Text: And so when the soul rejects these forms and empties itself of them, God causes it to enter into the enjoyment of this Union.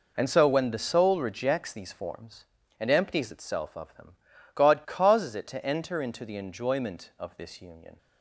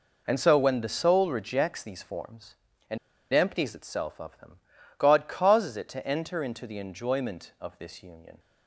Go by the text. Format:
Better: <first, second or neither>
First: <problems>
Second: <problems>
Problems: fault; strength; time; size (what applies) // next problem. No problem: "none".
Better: first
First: none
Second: pauses between "and" and "empties"; slight; at 2.9 s; 0.35 s long